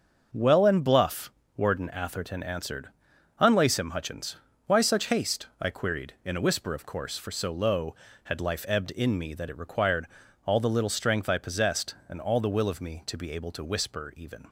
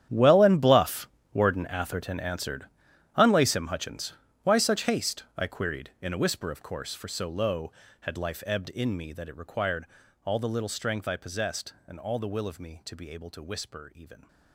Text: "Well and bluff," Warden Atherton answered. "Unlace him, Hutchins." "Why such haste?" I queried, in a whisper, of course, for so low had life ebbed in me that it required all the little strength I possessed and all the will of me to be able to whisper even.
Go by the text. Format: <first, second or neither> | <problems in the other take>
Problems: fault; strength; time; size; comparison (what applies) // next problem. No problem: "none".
first | gets quieter; strong; throughout; 16.5 dB // starts louder than the rest; strong; until 1.3 s; 10.5 dB; also in the first // pauses between "required" and "all"; slight; at 9.8 s; 0.36 s long; slight in the first